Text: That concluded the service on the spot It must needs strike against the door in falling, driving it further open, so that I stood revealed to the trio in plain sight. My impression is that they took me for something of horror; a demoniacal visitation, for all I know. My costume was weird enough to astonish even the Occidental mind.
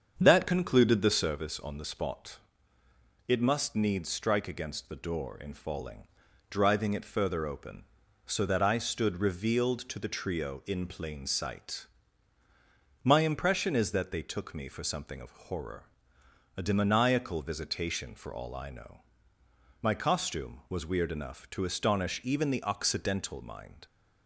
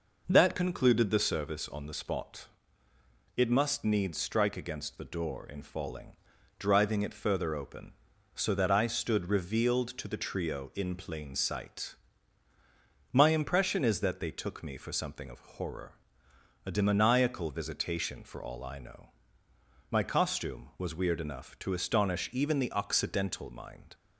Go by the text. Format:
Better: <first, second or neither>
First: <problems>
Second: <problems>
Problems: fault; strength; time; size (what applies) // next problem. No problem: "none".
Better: second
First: starts louder than the rest; strong; until 1.4 s; 7.5 dB // pauses between "spot" and "It"; noticeable; at 2.3 s; 0.88 s long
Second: pauses between "spot" and "It"; noticeable; at 2.4 s; 0.88 s long